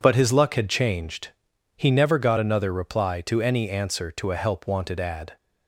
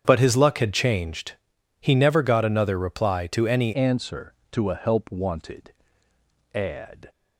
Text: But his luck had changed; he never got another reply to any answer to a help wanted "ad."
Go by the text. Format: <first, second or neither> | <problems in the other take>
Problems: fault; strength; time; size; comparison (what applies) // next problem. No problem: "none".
first | starts louder than the rest; strong; until 1.0 s; 8.5 dB // changes voice at "answer"; from 3.7 s on; 3.3 s long // pauses between "wanted" and "ad"; noticeable; at 5.7 s; 0.80 s long